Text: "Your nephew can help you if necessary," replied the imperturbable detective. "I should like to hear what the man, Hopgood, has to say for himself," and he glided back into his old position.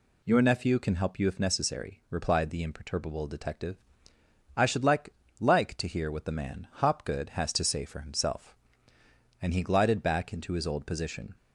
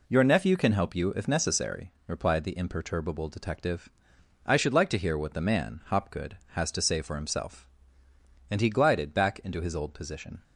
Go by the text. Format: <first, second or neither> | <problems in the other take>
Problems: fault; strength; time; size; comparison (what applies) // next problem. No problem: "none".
second | says "like" twice; at 5.4 s